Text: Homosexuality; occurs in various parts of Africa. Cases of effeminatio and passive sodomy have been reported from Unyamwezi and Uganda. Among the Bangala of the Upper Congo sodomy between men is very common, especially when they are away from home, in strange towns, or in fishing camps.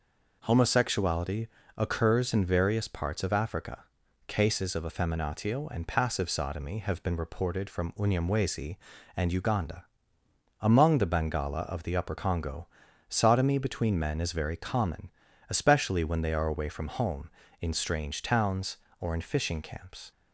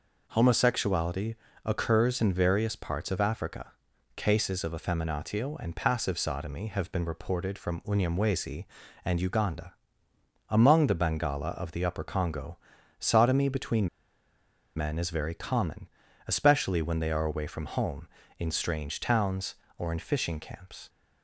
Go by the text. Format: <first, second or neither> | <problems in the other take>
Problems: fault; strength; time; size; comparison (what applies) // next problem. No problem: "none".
first | pauses between "Congo" and "sodomy"; at 12.5 s; 0.42 s long; also in the first // pauses between "between" and "men"; noticeable; at 13.8 s; 0.88 s long